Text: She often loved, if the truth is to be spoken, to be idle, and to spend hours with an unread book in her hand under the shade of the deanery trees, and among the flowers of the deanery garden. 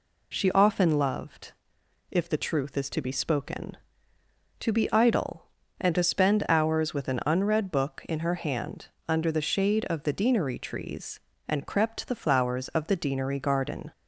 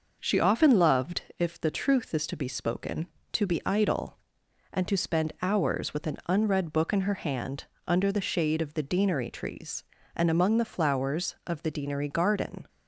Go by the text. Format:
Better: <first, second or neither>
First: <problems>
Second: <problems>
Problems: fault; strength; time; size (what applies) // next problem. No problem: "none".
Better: second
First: pauses between "hand" and "under"; slight; at 8.8 s; 0.20 s long // says "crept" for "among"; at 11.6 s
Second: pauses between "hand" and "under"; slight; at 7.6 s; 0.24 s long